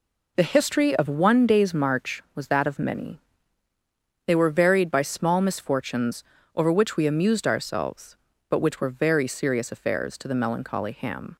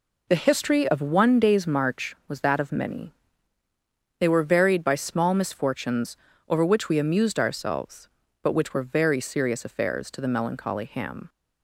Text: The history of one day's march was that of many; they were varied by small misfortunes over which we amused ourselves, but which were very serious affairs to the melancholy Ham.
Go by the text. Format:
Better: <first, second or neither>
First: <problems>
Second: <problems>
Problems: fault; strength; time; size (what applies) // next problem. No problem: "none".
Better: neither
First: pauses between "misfortunes" and "over"; slight; at 6.2 s; 0.32 s long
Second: pauses between "misfortunes" and "over"; slight; at 6.1 s; 0.32 s long